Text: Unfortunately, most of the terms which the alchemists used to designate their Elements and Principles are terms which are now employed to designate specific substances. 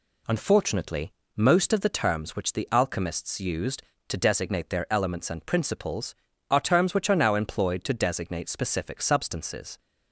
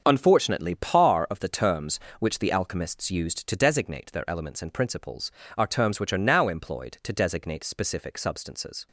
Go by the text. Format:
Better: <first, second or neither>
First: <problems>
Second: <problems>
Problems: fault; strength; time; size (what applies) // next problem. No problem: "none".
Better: first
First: none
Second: starts louder than the rest; until 1.0 s; 7 dB // says "par" for "most"; at 0.7 s